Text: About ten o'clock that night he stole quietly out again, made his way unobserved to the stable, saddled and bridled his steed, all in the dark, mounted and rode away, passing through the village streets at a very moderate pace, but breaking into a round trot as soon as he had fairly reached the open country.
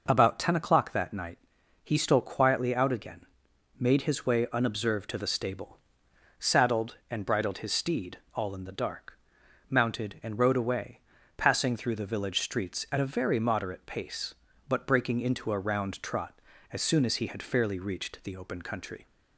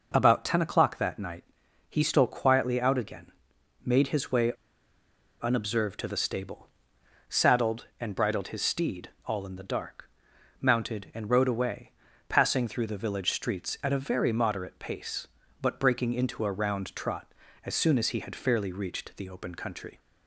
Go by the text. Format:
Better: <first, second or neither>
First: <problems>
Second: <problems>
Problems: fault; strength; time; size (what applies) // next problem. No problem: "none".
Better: first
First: pauses between "night" and "he"; noticeable; at 1.3 s; 0.46 s long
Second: pauses between "night" and "he"; noticeable; at 1.4 s; 0.46 s long // pauses between "way" and "unobserved"; noticeable; at 4.5 s; 0.90 s long